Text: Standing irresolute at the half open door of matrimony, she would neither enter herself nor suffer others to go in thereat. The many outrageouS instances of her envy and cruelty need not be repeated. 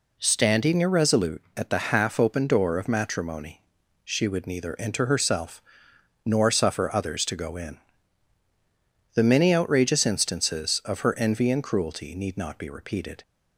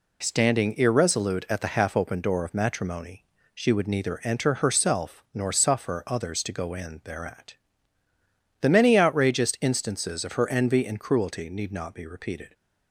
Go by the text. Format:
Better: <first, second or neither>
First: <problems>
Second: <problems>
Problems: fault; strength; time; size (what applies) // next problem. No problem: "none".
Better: second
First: pauses between "herself" and "nor"; noticeable; at 5.6 s; 0.64 s long // skips "thereat"; at 8.4 s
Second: none